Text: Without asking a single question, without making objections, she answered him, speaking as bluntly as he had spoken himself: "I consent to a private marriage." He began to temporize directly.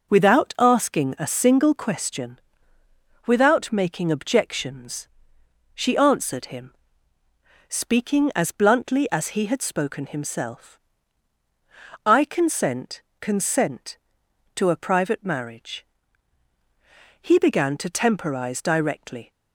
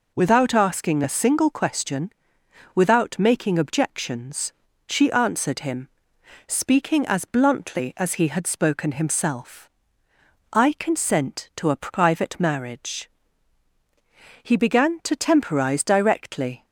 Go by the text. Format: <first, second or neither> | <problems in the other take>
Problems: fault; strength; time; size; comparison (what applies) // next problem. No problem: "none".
second | says "consent" twice; at 13.1 s